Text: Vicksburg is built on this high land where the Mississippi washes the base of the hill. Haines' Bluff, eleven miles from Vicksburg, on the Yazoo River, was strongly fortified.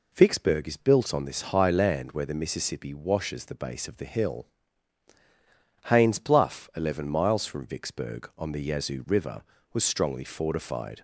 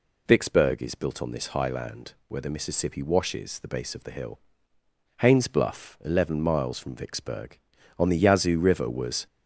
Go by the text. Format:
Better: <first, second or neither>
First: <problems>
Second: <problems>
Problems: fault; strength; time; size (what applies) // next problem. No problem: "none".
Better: first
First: none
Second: stops before "strongly fortified"; at 9.2 s